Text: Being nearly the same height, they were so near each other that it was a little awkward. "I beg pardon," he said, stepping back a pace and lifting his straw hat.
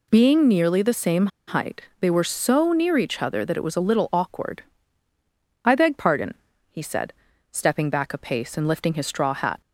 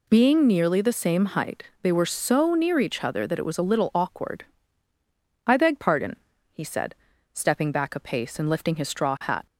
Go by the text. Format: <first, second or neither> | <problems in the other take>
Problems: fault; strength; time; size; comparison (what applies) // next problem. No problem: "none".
second | pauses between "same" and "height"; slight; at 1.2 s; 0.20 s long